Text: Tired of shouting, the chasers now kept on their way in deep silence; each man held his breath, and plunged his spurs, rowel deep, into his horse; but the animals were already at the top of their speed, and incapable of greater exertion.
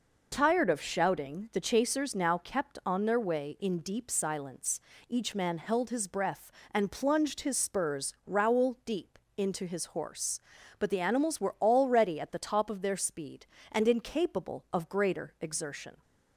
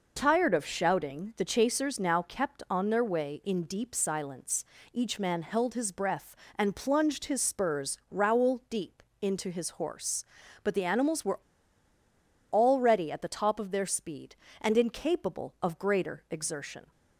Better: first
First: none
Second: pauses between "were" and "already"; at 11.3 s; 1.1 s long

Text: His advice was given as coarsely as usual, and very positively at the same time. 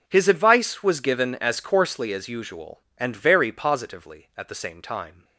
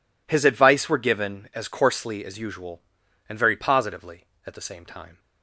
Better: first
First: none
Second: says "were" for "was"; at 0.8 s

